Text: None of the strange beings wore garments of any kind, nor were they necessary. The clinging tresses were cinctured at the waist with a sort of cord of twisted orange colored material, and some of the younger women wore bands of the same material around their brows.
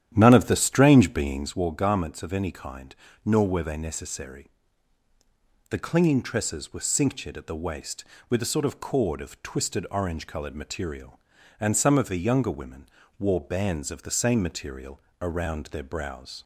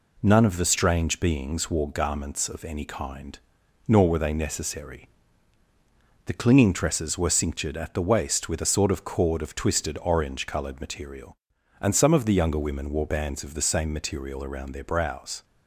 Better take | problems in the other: second | starts louder than the rest; strong; until 1.6 s; 11 dB // pauses between "women" and "wore"; slight; at 12.8 s; 0.32 s long // pauses between "material" and "around"; slight; at 15.0 s; 0.18 s long

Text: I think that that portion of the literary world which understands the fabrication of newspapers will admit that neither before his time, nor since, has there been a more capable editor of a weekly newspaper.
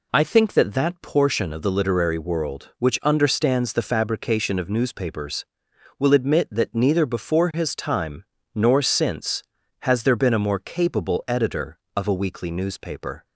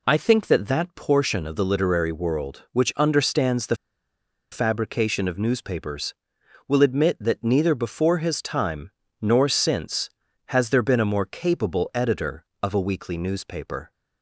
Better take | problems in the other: first | pauses between "the" and "fabrication"; noticeable; at 3.7 s; 0.76 s long

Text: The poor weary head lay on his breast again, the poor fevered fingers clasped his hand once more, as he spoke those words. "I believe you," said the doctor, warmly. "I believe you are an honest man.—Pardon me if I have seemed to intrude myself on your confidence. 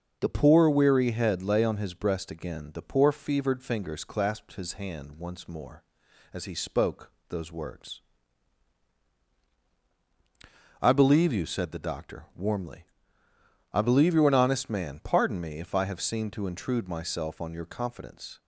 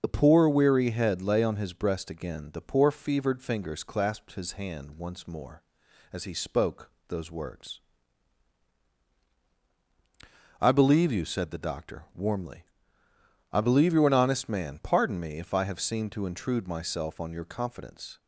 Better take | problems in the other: first | loses the start of "The"; at 0.0 s; 35 ms // starts louder than the rest; noticeable; until 1.0 s; 6 dB; noticeable in the first // pauses between "spoke" and "those"; slight; at 6.9 s; 0.16 s long; slight in the first

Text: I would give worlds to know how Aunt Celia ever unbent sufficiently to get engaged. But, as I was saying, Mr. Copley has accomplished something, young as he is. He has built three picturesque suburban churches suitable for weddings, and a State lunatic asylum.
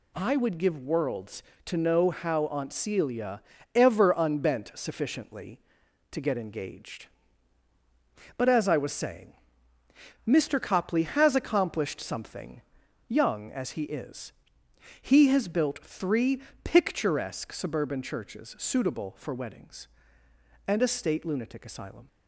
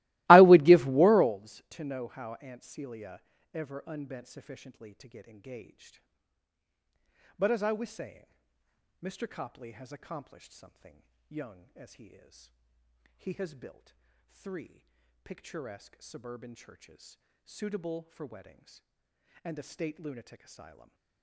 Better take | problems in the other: first | starts louder than the rest; strong; until 1.4 s; 20.5 dB // pauses between "Celia" and "ever"; slight; at 3.2 s; 0.32 s long; slight in the first // pauses between "built" and "three"; slight; at 13.9 s; 0.34 s long // pauses between "three" and "picturesque"; at 14.8 s; 0.38 s long; slight in the first // pauses between "churches" and "suitable"; slight; at 17.1 s; 0.26 s long // stays silent after the last word; slight; from 20.6 s on; 0.6 s long

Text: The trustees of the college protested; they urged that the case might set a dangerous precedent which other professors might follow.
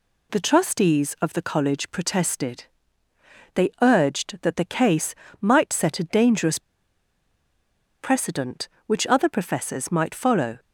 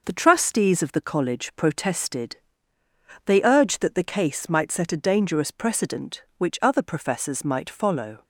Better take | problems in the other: second | pauses between "case" and "might"; slight; at 5.1 s; 0.26 s long // pauses between "dangerous" and "precedent"; strong; at 6.5 s; 1.3 s long

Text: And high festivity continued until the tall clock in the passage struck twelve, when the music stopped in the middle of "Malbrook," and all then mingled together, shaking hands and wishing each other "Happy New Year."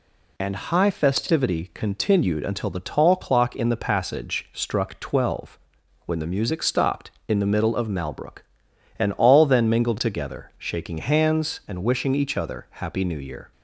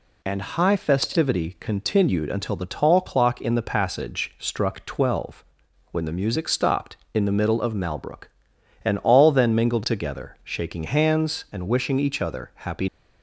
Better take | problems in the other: first | stops before "New Year"; at 12.8 s

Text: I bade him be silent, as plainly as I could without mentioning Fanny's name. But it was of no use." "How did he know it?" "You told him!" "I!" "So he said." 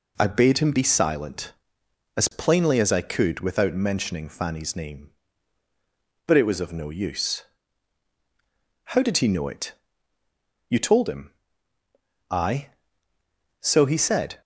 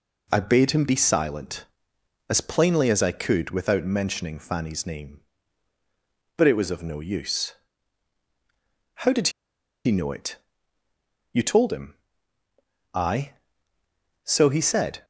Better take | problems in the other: first | pauses between "did" and "he"; noticeable; at 9.2 s; 0.56 s long

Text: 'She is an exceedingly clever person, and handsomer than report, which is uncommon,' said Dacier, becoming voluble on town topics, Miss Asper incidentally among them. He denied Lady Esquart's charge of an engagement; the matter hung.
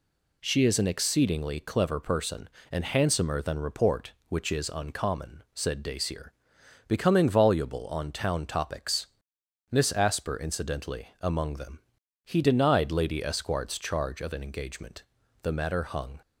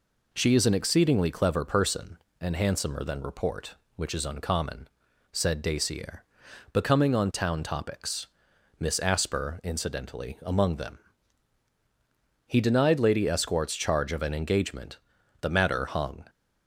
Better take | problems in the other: first | skips "voluble"; at 7.1 s

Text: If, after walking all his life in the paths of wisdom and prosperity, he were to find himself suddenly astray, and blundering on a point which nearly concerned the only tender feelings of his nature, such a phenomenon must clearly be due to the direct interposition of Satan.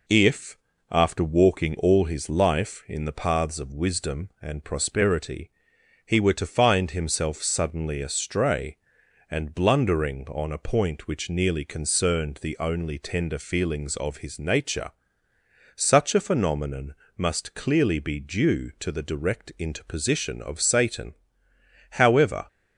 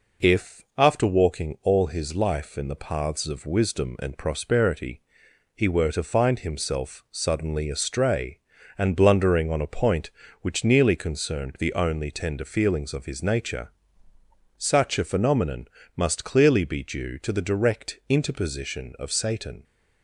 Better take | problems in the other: second | pauses between "phenomenon" and "must"; slight; at 16.9 s; 0.22 s long; slight in the second // goes on to say "However"; from 21.9 s on; 0.56 s long

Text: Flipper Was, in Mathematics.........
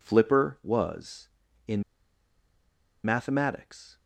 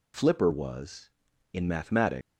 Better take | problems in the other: second | pauses between "in" and "Mathematics"; at 1.8 s; 1.2 s long

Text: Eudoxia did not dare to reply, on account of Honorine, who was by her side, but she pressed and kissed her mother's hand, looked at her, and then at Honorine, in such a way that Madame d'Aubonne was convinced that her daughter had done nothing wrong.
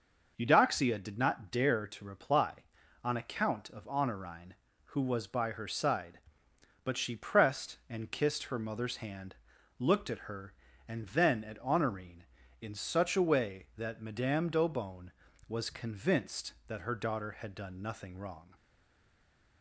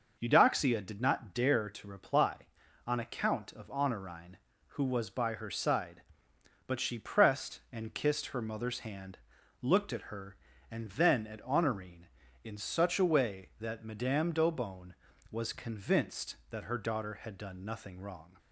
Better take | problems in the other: second | stays silent after the last word; from 18.5 s on; 1.1 s long

